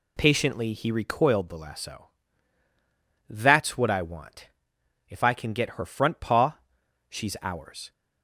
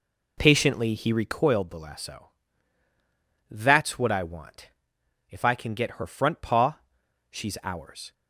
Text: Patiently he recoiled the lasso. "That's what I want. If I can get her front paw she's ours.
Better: first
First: pauses between "paw" and "she's"; noticeable; at 6.5 s; 0.52 s long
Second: starts louder than the rest; slight; until 1.3 s; 3.5 dB // pauses between "paw" and "she's"; noticeable; at 6.7 s; 0.52 s long

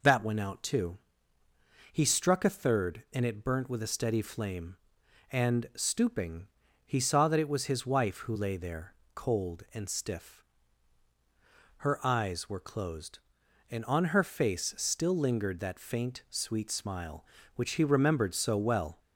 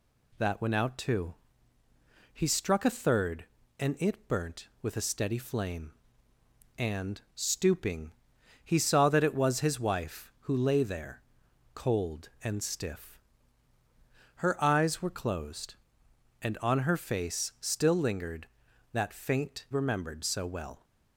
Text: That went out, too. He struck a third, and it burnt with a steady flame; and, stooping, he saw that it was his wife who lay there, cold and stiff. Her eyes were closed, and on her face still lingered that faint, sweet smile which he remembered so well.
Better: first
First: none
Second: skips "sweet smile which he"; at 19.6 s

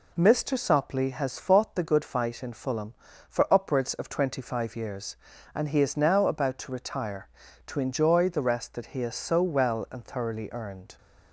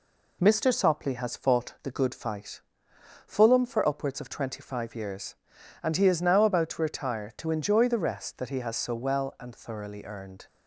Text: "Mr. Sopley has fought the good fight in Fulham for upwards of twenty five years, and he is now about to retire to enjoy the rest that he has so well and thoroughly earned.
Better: first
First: none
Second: skips "in"; at 2.9 s

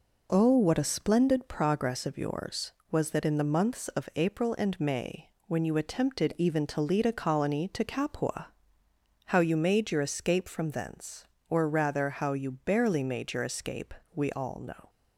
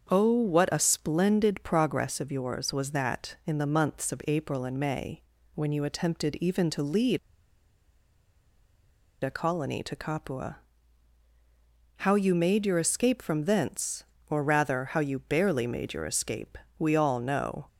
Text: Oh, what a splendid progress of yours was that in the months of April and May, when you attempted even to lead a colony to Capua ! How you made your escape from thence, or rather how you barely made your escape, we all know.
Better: first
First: none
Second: starts louder than the rest; until 1.1 s; 7 dB // pauses between "lead" and "a"; strong; at 7.1 s; 2.0 s long

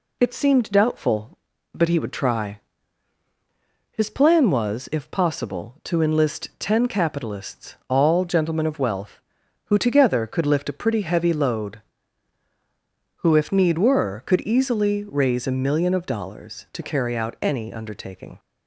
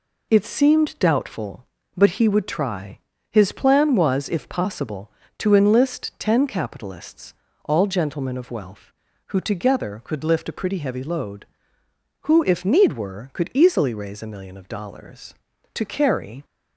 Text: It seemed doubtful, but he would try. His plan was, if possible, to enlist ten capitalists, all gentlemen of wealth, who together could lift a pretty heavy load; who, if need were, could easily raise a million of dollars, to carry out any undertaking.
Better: first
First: none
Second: stops before "out any undertaking"; at 16.4 s

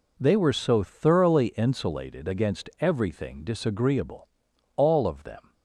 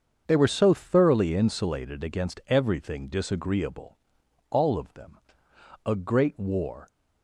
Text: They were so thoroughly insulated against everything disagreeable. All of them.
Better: first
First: none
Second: starts louder than the rest; until 1.2 s; 7 dB // goes on to say "A great war"; noticeable; from 5.8 s on; 1.0 s long

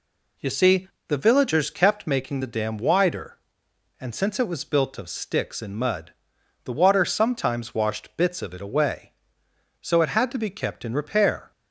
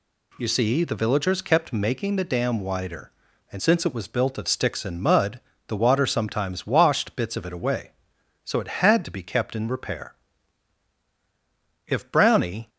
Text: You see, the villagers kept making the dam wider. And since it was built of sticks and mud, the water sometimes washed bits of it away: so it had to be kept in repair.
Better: first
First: none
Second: goes on to say "If Brownie"; noticeable; from 11.8 s on; 0.82 s long

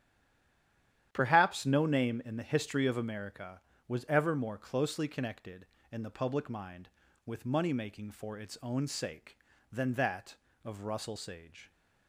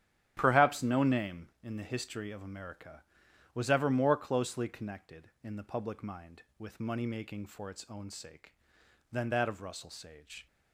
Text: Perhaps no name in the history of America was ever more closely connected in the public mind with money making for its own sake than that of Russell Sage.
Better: second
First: stays silent before the first word; until 1.1 s; 1.1 s long // starts louder than the rest; strong; until 2.1 s; 10.5 dB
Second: starts louder than the rest; strong; until 1.3 s; 10.5 dB

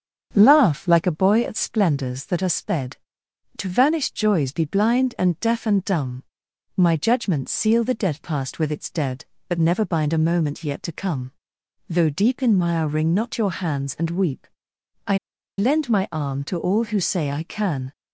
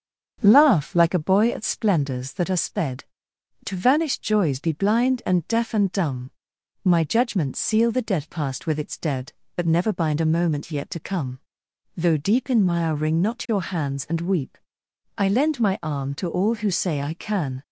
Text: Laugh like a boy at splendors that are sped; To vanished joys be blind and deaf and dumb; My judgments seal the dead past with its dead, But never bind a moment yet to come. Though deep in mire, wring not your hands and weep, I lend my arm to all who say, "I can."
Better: second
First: starts louder than the rest; strong; until 1.3 s; 7.5 dB // pauses between "I" and "lend"; at 15.1 s; 0.40 s long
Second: starts louder than the rest; strong; until 1.4 s; 7.5 dB

